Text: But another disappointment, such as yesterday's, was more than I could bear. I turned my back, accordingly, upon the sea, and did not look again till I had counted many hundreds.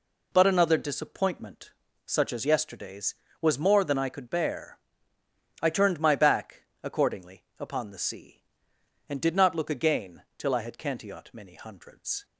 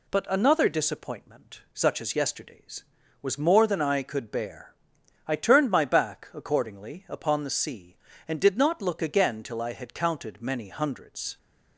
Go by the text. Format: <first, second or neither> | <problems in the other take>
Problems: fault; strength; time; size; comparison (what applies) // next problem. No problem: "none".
second | says "cantiot" for "counted"; at 10.7 s